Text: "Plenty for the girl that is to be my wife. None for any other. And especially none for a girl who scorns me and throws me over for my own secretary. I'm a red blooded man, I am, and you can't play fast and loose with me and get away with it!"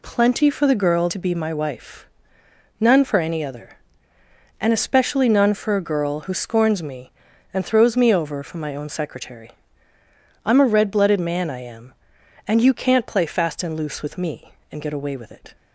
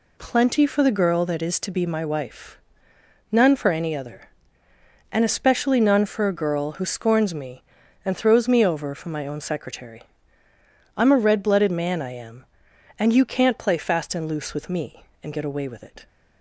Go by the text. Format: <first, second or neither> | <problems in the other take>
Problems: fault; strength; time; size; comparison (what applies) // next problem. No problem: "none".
second | skips "that is"; at 1.0 s